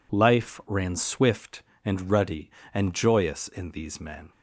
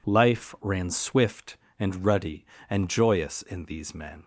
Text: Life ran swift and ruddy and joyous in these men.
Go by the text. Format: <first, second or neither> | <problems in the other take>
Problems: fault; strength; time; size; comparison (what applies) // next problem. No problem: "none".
neither | none